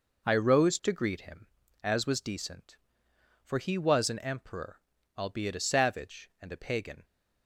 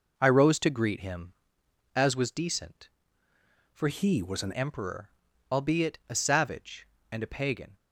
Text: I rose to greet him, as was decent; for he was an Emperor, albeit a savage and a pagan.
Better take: first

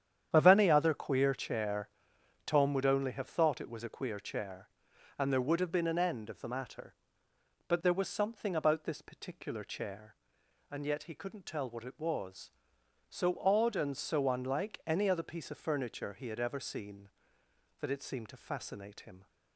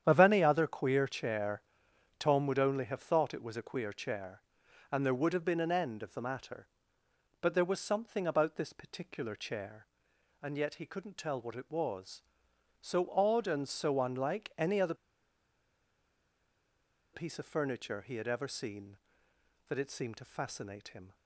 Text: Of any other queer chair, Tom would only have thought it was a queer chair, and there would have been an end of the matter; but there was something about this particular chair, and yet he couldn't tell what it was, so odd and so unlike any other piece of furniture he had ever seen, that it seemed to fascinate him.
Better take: first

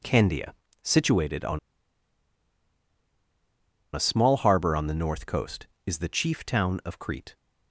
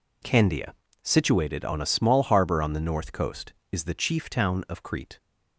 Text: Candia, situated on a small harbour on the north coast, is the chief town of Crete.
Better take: second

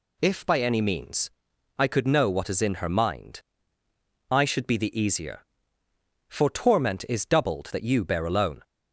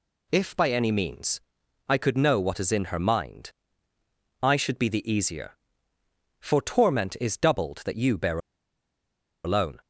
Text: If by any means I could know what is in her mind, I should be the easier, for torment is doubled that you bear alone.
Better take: first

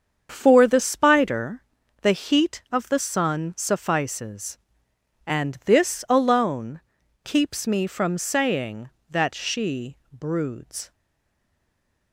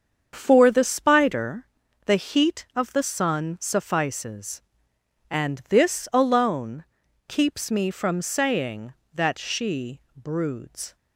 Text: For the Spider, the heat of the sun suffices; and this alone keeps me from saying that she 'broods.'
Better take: second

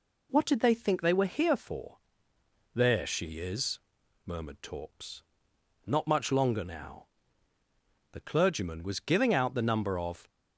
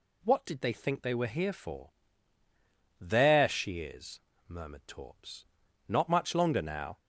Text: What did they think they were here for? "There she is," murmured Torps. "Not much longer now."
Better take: second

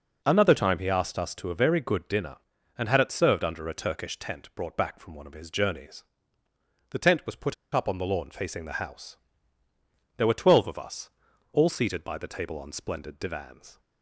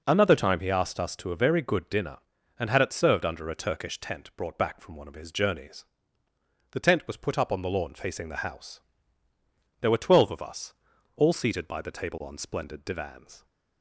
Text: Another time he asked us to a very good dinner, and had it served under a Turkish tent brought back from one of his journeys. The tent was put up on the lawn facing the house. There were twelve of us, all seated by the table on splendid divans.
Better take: second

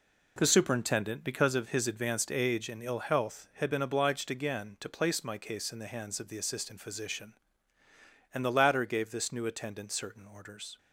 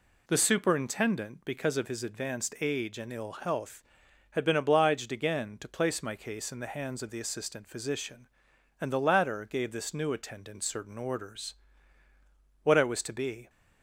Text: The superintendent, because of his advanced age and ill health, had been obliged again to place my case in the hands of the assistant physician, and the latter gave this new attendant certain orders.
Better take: first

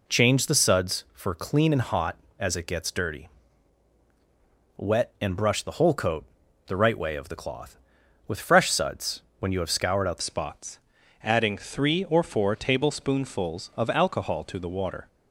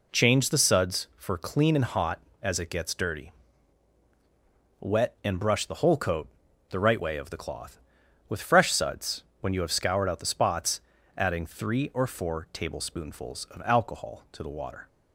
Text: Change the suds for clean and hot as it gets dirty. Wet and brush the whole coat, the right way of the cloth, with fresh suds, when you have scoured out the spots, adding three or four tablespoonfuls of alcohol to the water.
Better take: second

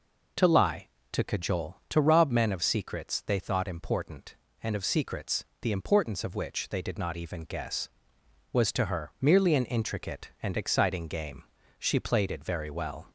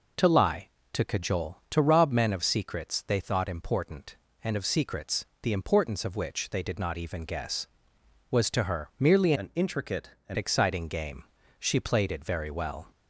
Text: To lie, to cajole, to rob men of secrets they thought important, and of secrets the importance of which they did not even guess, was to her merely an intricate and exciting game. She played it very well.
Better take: first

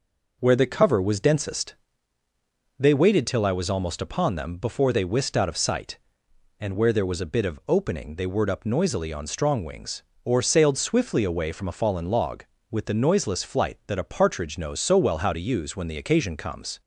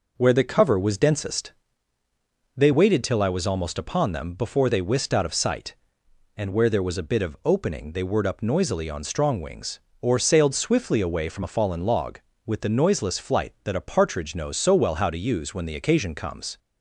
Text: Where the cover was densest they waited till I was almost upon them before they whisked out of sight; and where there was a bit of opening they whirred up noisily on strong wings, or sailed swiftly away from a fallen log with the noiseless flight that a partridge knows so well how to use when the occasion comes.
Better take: neither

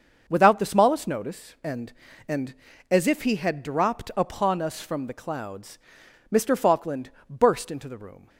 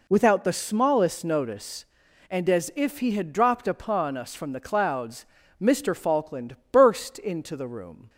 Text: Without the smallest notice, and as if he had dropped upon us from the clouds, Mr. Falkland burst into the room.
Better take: second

